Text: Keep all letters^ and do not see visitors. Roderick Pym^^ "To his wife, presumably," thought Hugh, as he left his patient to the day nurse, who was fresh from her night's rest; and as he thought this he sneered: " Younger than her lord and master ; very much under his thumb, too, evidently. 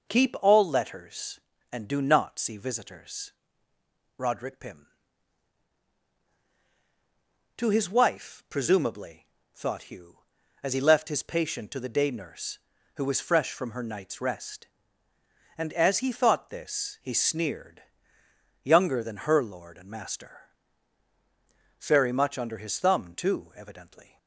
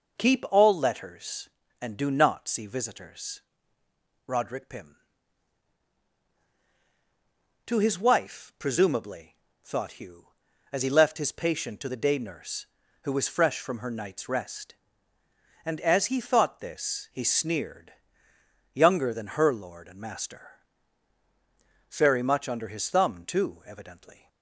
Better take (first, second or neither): neither